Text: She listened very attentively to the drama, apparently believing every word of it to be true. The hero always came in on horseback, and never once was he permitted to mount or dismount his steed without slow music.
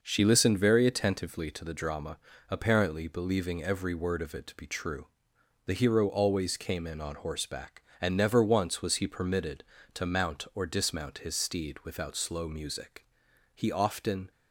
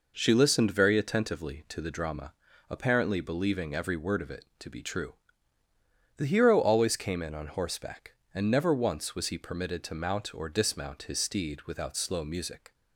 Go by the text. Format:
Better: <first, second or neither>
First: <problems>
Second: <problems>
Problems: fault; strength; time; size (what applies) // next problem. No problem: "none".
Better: second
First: goes on to say "He often"; noticeable; from 13.5 s on; 0.76 s long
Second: none